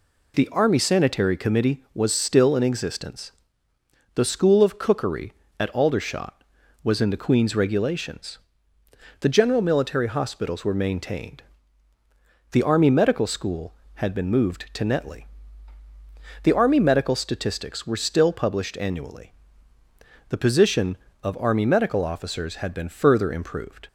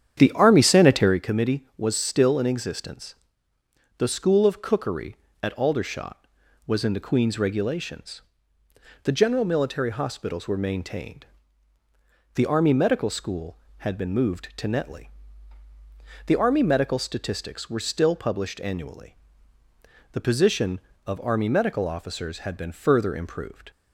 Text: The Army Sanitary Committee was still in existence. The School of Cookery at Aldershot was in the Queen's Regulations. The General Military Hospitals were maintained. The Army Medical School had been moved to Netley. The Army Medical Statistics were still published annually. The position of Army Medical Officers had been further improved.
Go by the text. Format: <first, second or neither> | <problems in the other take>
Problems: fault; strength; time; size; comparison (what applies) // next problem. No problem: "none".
first | starts louder than the rest; strong; until 1.2 s; 9 dB